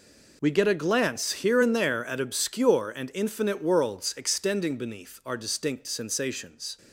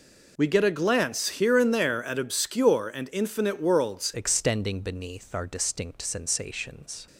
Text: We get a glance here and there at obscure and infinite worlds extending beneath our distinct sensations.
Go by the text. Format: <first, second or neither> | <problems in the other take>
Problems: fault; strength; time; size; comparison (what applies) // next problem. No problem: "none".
first | changes voice at "extending"; from 4.1 s on; 2.9 s long